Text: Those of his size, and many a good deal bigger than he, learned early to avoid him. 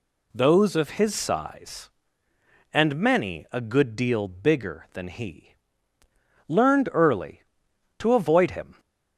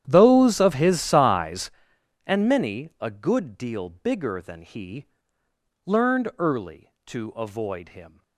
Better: first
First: none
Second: starts louder than the rest; strong; until 1.8 s; 10.5 dB

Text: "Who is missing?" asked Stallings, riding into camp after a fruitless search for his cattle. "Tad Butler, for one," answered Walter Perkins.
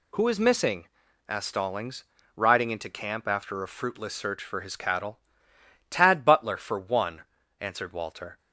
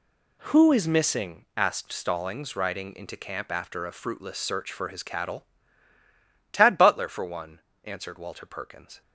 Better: second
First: stops before "Perkins"; at 8.3 s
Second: none

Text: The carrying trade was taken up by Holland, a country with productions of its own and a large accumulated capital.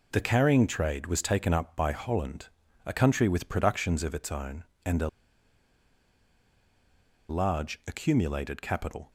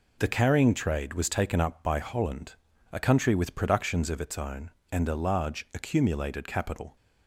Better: second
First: pauses between "a" and "large"; strong; at 5.0 s; 2.2 s long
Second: none

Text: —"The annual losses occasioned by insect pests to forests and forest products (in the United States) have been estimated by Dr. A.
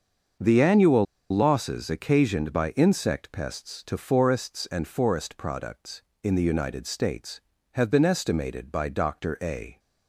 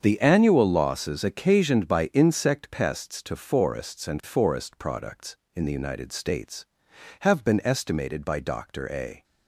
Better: second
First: starts louder than the rest; until 1.6 s; 6.5 dB // pauses between "annual" and "losses"; slight; at 1.0 s; 0.27 s long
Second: starts louder than the rest; strong; until 1.0 s; 7 dB

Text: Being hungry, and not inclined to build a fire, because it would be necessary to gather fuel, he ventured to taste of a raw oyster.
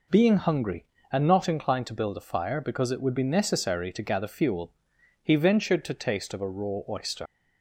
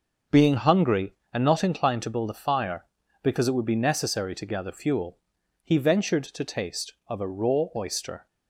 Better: second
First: leaves "oyster" unfinished; at 7.2 s; 75 ms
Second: none

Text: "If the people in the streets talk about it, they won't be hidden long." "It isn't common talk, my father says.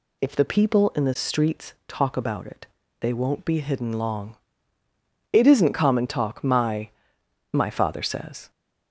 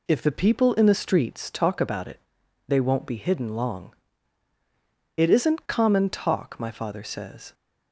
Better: second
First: pauses between "streets" and "talk"; slight; at 1.7 s; 0.16 s long // says "my" twice; at 7.5 s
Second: none

